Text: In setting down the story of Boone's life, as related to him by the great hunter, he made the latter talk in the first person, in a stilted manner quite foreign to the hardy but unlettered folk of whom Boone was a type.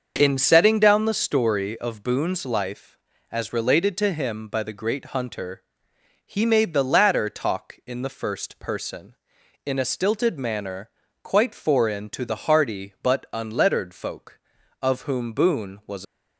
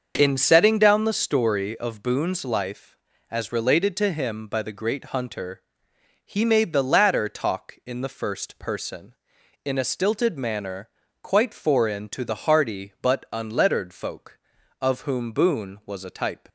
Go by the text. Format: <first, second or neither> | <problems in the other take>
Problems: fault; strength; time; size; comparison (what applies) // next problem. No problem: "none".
second | starts louder than the rest; until 1.1 s; 6.5 dB; also in the second // pauses between "manner" and "quite"; slight; at 10.8 s; 0.32 s long; slight in the second // stops before "a type"; at 16.0 s